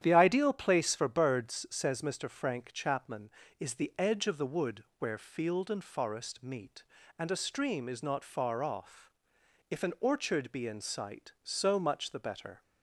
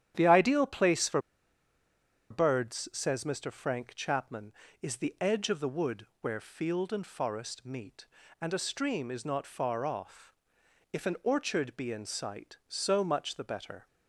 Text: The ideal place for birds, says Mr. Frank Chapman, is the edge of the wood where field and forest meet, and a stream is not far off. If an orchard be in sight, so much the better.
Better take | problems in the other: first | starts louder than the rest; strong; until 1.1 s; 10 dB; strong in the first // pauses between "for" and "birds"; at 1.1 s; 1.1 s long // pauses between "wood" and "where"; slight; at 6.0 s; 0.16 s long; slight in the first

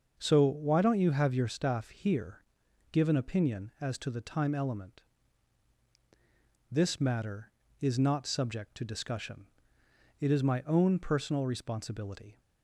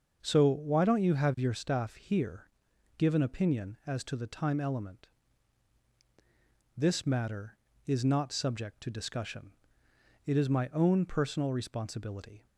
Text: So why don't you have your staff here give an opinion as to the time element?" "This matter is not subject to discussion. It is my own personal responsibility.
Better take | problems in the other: neither | starts louder than the rest; the same in both // pauses between "here" and "give"; noticeable; the same in both

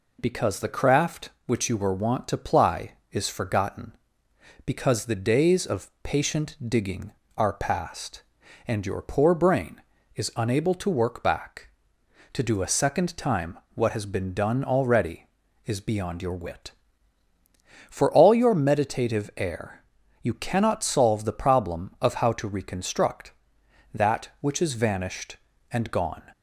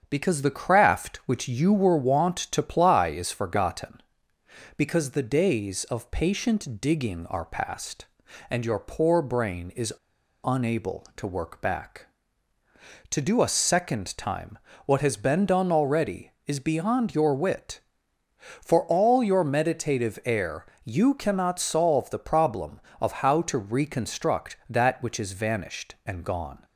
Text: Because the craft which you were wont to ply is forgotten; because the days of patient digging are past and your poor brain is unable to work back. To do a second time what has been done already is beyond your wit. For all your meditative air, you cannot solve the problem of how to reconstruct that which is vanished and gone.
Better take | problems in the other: first | starts louder than the rest; strong; until 1.1 s; 7.5 dB // pauses between "is" and "unable"; noticeable; at 9.9 s; 0.50 s long // pauses between "time" and "what"; slight; at 14.5 s; 0.28 s long; slight in the first

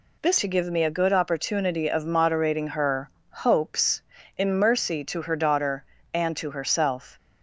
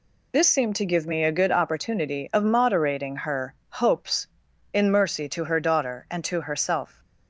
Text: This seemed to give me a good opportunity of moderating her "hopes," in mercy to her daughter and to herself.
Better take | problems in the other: second | skips "seemed"; at 0.3 s // pauses between "her" and "hopes"; slight; at 3.0 s; 0.22 s long; slight in the second

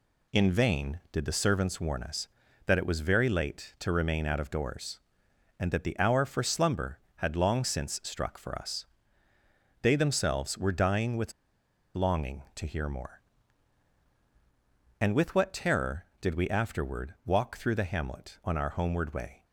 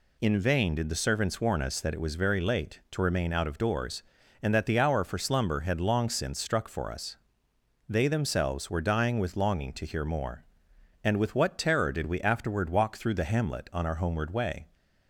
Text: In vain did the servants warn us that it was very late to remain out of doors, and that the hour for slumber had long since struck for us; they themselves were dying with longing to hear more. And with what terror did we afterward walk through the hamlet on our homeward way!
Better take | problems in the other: second | pauses between "with" and "longing"; noticeable; at 11.3 s; 0.62 s long

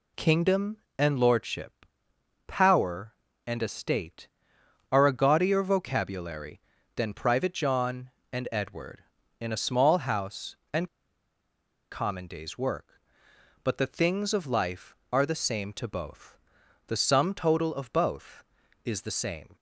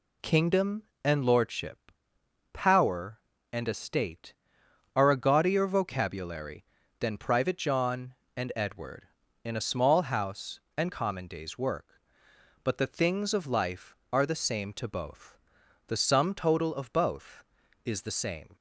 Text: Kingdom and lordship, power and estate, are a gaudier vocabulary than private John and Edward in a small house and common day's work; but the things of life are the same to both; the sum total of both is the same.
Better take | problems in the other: second | pauses between "and" and "common"; at 10.8 s; 1.0 s long

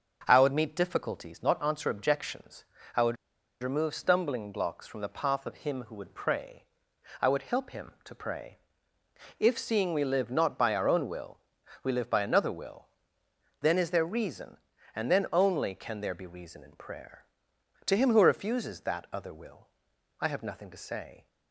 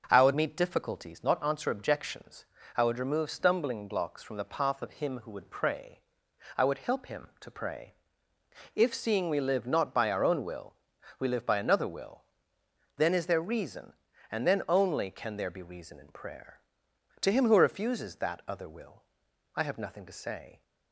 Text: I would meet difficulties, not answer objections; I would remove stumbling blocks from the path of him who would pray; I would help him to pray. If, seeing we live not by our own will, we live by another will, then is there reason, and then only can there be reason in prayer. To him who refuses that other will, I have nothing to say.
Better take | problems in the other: second | pauses between "would" and "remove"; noticeable; at 3.1 s; 0.46 s long

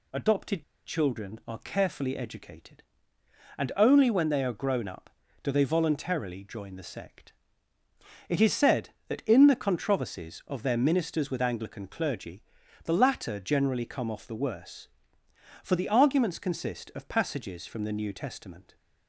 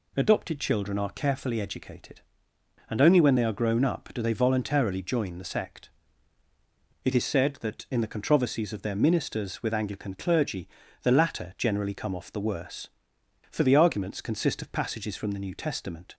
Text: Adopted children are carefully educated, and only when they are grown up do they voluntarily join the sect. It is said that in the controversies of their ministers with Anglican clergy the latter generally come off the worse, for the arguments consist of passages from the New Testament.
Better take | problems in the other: second | pauses between "Adopted" and "children"; slight; at 0.6 s; 0.21 s long // pauses between "clergy" and "the"; at 12.4 s; 0.40 s long; slight in the second

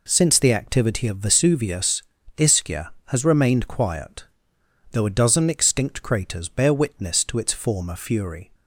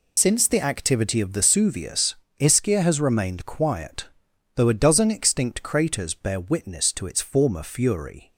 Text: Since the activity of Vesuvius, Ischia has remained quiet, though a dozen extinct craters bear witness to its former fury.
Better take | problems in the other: first | loses the start of "Since"; at 0.1 s; 55 ms

